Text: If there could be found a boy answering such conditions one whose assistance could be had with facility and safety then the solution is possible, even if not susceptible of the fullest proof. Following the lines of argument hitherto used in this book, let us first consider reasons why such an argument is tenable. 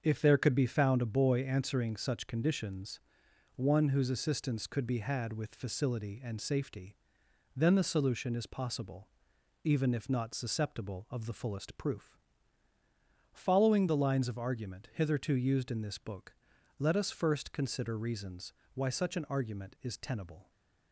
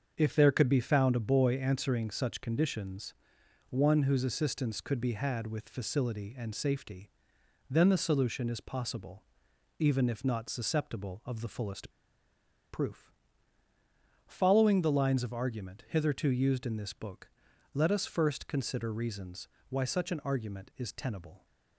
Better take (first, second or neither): first